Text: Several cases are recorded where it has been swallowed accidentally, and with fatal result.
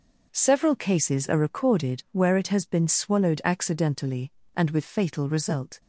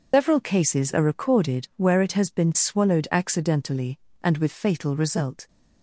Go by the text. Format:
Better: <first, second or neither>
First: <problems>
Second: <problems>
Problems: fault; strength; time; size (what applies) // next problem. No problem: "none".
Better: first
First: none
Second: loses the start of "Several"; at 0.1 s; 180 ms